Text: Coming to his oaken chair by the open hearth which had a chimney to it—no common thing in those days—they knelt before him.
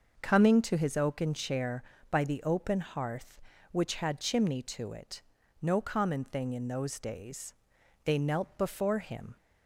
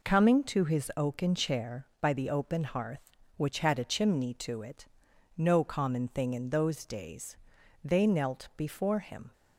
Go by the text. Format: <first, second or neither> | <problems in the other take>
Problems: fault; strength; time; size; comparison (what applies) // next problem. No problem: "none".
second | starts louder than the rest; noticeable; until 1.2 s; 6 dB // skips "a"; at 4.2 s